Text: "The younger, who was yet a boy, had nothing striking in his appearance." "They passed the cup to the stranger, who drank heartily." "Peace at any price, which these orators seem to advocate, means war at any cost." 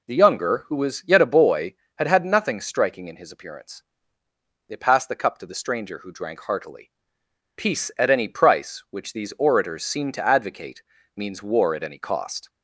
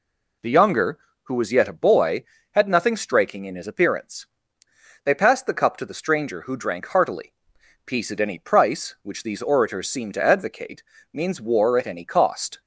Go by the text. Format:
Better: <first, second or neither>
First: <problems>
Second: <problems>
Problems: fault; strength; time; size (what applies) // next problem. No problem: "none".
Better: second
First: says "had" twice; at 2.0 s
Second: none